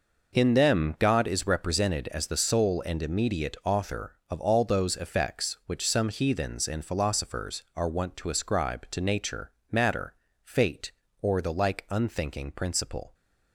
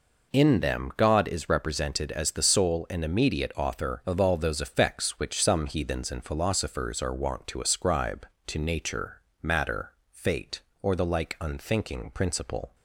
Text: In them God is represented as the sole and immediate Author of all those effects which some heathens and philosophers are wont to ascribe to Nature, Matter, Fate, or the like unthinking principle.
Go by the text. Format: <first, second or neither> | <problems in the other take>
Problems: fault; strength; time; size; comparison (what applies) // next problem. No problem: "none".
neither | none